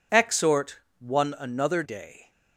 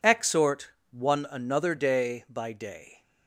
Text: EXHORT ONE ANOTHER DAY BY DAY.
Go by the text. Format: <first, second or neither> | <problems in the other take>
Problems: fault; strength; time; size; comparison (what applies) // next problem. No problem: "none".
second | pauses between "EXHORT" and "ONE"; slight; at 0.7 s; 0.18 s long; slight in the second // skips "DAY BY"; at 1.8 s